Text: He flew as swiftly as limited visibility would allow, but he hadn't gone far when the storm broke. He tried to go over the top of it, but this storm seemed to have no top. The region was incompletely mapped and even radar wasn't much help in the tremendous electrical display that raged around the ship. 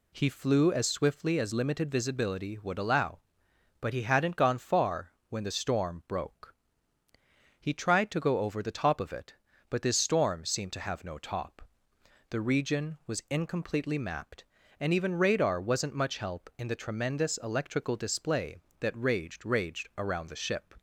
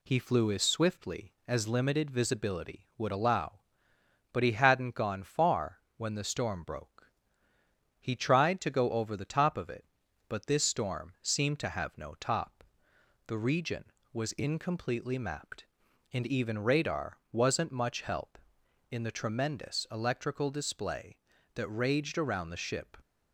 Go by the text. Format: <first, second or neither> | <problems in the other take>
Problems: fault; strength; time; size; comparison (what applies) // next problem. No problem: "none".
second | pauses between "far" and "when"; slight; at 5.1 s; 0.16 s long; slight in the second // says "raged" twice; at 19.4 s